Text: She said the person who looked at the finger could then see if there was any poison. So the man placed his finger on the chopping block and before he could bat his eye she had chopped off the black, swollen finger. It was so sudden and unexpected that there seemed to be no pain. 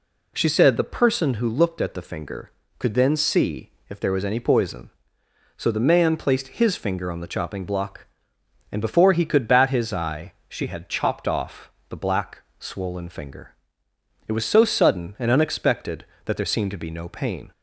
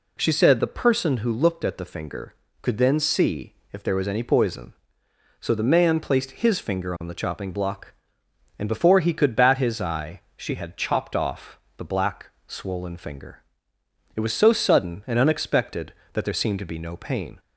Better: neither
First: pauses between "see" and "if"; slight; at 3.7 s; 0.18 s long // pauses between "eye" and "she"; slight; at 10.3 s; 0.16 s long // pauses between "off" and "the"; slight; at 11.6 s; 0.20 s long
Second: pauses between "see" and "if"; slight; at 3.5 s; 0.18 s long // pauses between "eye" and "she"; slight; at 10.1 s; 0.16 s long // pauses between "off" and "the"; slight; at 11.5 s; 0.20 s long

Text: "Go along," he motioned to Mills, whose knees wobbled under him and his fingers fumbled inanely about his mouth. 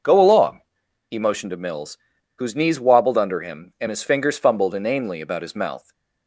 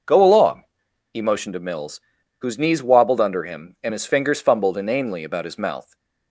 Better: neither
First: none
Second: none

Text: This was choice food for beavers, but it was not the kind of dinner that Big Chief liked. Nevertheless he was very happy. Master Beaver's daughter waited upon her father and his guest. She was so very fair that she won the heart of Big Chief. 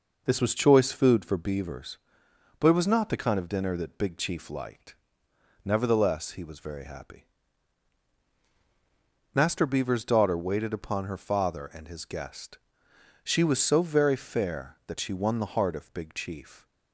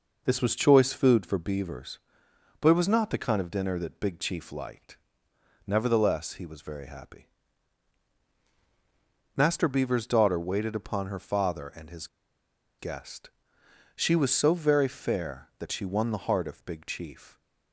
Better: first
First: none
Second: pauses between "his" and "guest"; noticeable; at 12.0 s; 0.72 s long

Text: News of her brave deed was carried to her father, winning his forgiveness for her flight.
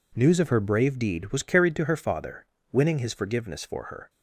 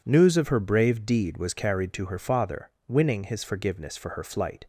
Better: second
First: stops before "flight"; at 4.0 s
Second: none

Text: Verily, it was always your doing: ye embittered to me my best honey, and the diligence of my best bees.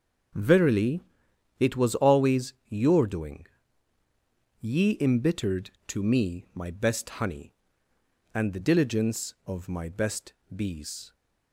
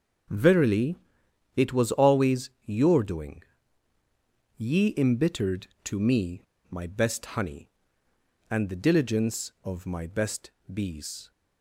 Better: first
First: starts louder than the rest; until 1.9 s; 6.5 dB // pauses between "always" and "your"; slight; at 2.5 s; 0.16 s long // pauses between "best" and "bees"; slight; at 10.3 s; 0.22 s long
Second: starts louder than the rest; until 1.8 s; 6.5 dB // pauses between "always" and "your"; slight; at 2.4 s; 0.16 s long // pauses between "me" and "my"; slight; at 6.4 s; 0.27 s long // pauses between "best" and "bees"; slight; at 10.5 s; 0.22 s long

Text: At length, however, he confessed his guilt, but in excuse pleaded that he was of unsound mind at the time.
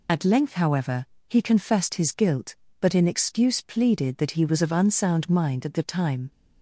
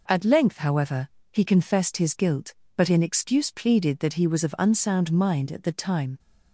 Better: second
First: loses the start of "At"; at 0.0 s; 35 ms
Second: none

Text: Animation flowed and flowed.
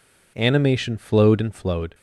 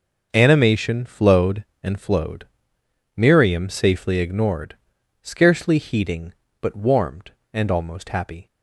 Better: first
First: none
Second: starts louder than the rest; noticeable; until 1.3 s; 6 dB // goes on to say "Miriam safely ignored scarcely heeding but warmed and almost happy"; strong; from 3.1 s on; 5.3 s long

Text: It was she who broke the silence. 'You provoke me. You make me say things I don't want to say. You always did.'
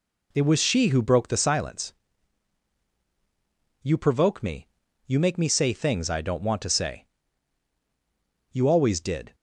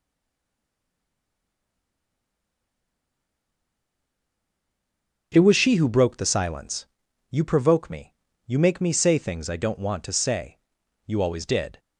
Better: first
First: none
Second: stays silent before the first word; strong; until 5.3 s; 5.3 s long // starts louder than the rest; until 6.3 s; 7 dB

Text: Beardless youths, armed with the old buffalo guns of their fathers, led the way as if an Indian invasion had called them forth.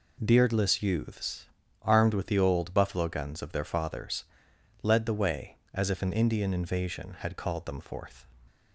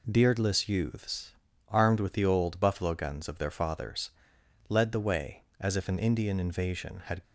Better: first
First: none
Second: stops before "called them forth"; at 7.2 s

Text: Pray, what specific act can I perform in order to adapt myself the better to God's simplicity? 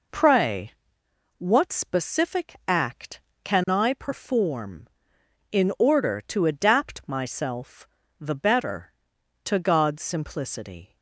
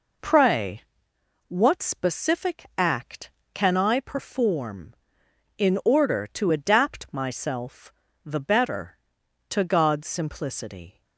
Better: neither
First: pauses between "myself" and "the"; slight; at 7.8 s; 0.32 s long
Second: pauses between "myself" and "the"; slight; at 7.9 s; 0.32 s long

